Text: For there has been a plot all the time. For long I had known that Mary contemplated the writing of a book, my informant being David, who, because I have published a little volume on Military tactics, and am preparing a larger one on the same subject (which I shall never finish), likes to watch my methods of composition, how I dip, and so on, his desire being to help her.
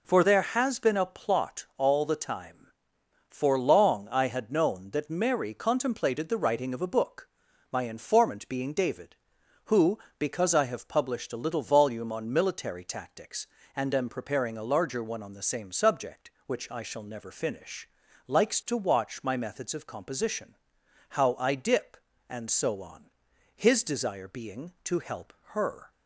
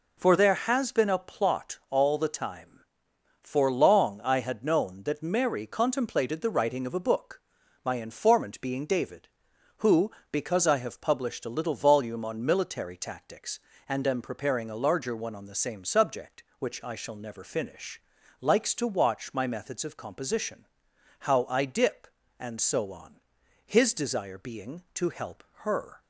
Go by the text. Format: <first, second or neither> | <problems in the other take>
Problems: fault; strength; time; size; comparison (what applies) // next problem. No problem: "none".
neither | pauses between "help" and "her"; slight; the same in both